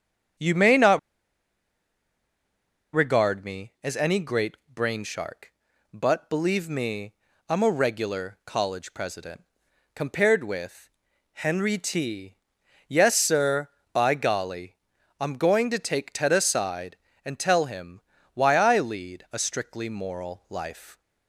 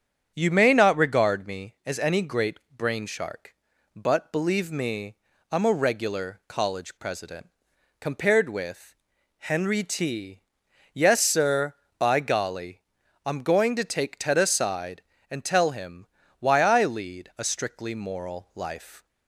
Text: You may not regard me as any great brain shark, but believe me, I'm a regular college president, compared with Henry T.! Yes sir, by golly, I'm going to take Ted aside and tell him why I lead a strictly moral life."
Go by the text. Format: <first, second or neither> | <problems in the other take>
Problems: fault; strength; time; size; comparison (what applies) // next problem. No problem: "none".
second | starts louder than the rest; strong; until 3.3 s; 8 dB; strong in the second // pauses between "not" and "regard"; strong; at 0.9 s; 1.9 s long // pauses between "great" and "brain"; slight; at 4.5 s; 0.18 s long; slight in the second // pauses between "with" and "Henry"; at 10.8 s; 0.44 s long; also in the second // pauses between "him" and "why"; slight; at 17.9 s; 0.34 s long; slight in the second